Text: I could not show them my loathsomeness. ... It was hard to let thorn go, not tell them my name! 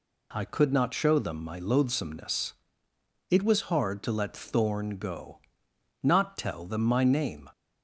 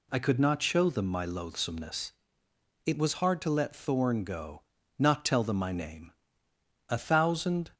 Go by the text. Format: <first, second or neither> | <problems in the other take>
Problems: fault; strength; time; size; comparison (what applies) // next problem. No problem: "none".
first | goes on to say "A thousand"; noticeable; from 6.8 s on; 0.82 s long